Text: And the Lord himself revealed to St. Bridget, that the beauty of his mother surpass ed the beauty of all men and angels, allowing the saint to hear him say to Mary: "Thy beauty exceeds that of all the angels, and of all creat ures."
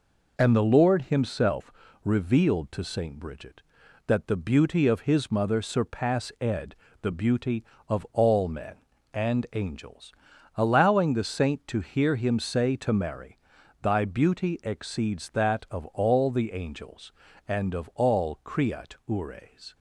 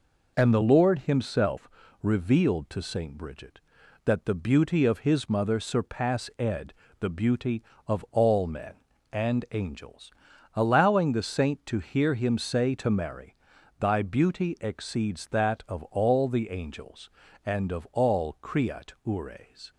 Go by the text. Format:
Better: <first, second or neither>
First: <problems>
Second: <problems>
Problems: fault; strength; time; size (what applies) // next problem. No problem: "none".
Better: neither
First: pauses between "himself" and "revealed"; slight; at 1.7 s; 0.30 s long // pauses between "ed" and "the"; slight; at 6.7 s; 0.28 s long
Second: pauses between "himself" and "revealed"; slight; at 1.6 s; 0.32 s long // pauses between "ed" and "the"; slight; at 6.7 s; 0.28 s long